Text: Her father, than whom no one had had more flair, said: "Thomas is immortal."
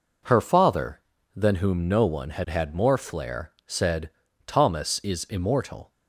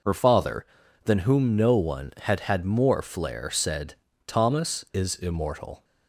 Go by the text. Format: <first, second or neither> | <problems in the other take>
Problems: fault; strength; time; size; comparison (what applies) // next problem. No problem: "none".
neither | none